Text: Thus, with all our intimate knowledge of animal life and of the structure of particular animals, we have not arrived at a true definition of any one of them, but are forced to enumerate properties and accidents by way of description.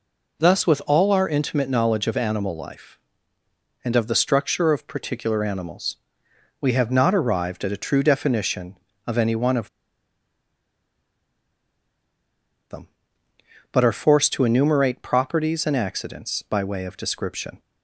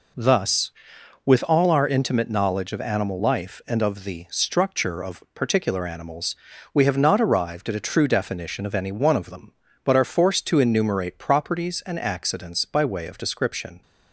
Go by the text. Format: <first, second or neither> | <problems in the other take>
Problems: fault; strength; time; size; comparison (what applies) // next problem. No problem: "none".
second | pauses between "of" and "them"; strong; at 9.6 s; 3.0 s long